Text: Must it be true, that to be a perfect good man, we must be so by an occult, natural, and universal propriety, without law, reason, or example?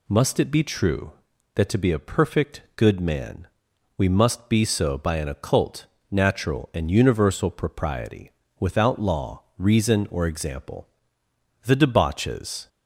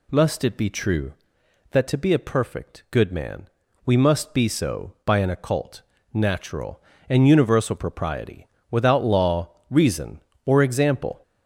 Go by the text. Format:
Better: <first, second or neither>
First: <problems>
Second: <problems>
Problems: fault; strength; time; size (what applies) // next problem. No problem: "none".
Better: second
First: goes on to say "The debauches"; noticeable; from 11.6 s on; 1.0 s long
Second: none